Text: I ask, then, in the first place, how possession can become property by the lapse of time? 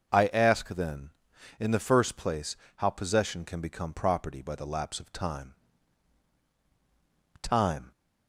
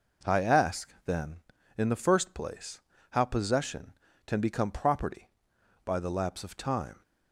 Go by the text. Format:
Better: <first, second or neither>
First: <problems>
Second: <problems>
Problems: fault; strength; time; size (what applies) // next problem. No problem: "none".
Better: second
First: starts louder than the rest; noticeable; until 1.6 s; 6 dB // says "time" twice; at 7.4 s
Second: none